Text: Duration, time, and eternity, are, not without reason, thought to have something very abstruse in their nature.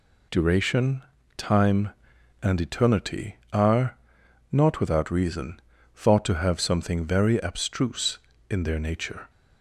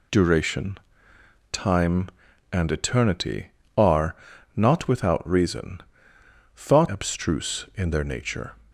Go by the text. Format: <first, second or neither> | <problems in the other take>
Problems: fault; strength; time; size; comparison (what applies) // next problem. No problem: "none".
first | skips "to have something very"; at 6.8 s